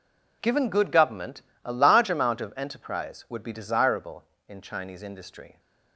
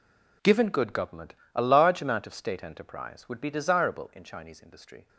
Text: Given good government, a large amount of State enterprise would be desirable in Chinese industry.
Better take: second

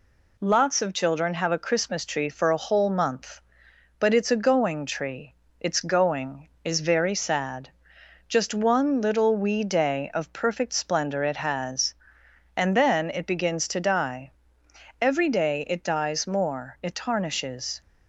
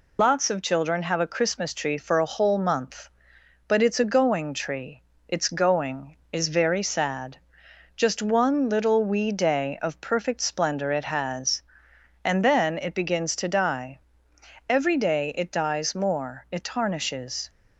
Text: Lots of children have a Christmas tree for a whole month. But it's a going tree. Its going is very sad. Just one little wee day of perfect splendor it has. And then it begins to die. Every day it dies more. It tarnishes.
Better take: first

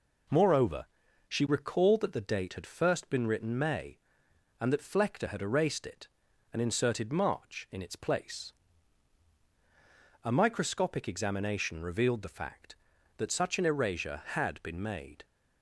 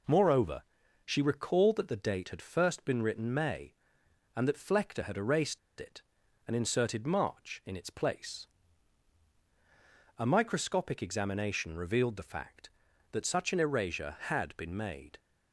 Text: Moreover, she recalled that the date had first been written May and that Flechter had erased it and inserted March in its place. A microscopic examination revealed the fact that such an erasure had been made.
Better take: first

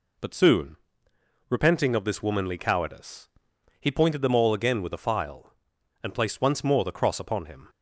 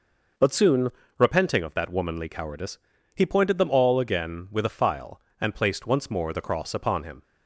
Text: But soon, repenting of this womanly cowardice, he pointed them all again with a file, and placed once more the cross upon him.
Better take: first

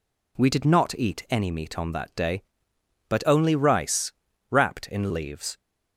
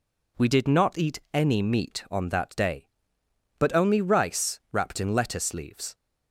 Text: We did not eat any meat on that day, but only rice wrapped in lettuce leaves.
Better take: second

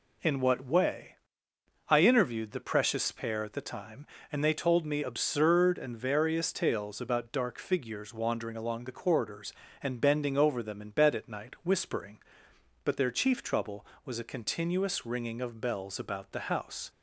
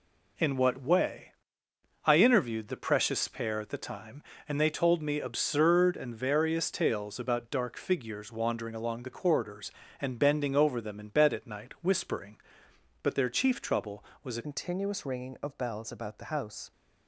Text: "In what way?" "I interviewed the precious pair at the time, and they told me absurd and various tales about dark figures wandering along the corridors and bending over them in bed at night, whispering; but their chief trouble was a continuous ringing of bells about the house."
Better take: first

